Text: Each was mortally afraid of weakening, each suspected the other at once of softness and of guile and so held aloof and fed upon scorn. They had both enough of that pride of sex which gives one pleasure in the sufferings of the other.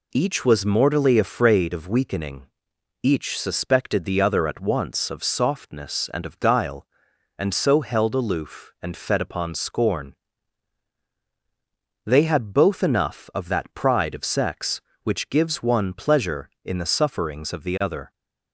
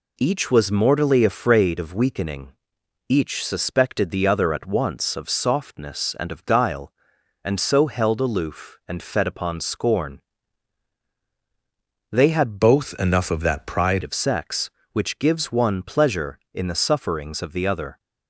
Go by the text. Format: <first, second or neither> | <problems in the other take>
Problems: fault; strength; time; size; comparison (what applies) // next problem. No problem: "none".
first | changes voice from "both" to "pride"; from 12.6 to 14.0 s; 1.4 s long